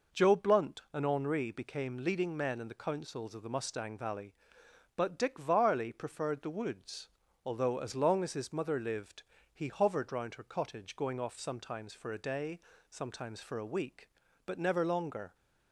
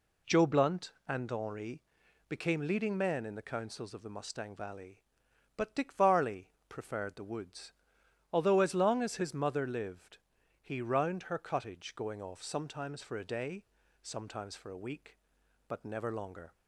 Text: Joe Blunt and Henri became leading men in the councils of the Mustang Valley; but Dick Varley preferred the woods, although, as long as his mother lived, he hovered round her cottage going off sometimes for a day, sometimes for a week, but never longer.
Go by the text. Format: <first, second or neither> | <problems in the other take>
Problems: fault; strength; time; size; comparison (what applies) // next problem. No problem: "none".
first | pauses between "Henri" and "became"; noticeable; at 1.8 s; 0.46 s long // pauses between "Varley" and "preferred"; slight; at 6.4 s; 0.20 s long // skips "hovered"; at 10.8 s